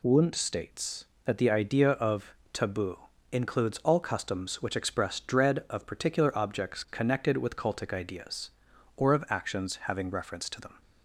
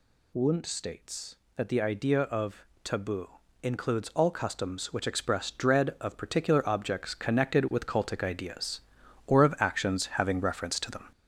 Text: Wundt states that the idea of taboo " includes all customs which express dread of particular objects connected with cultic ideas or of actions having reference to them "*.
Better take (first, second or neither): first